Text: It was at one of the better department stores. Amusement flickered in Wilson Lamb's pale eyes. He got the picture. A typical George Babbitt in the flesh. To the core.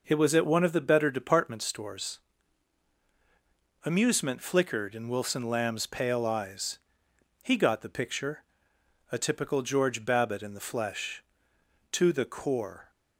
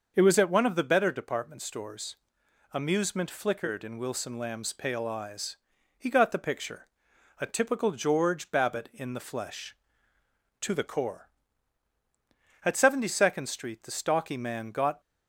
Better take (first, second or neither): first